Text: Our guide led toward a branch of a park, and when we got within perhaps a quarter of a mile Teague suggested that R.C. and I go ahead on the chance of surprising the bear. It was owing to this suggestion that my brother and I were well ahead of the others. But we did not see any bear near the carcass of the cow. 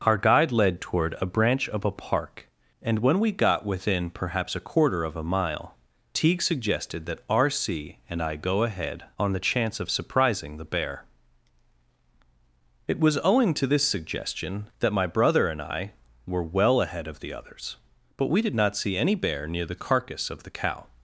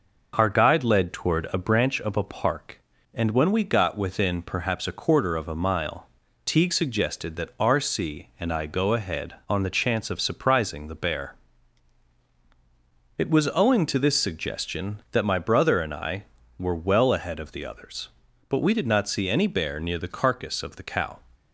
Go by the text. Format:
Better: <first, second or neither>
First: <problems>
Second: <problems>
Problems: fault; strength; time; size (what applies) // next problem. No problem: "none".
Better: neither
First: pauses between "mile" and "Teague"; slight; at 5.7 s; 0.36 s long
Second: pauses between "mile" and "Teague"; slight; at 6.0 s; 0.36 s long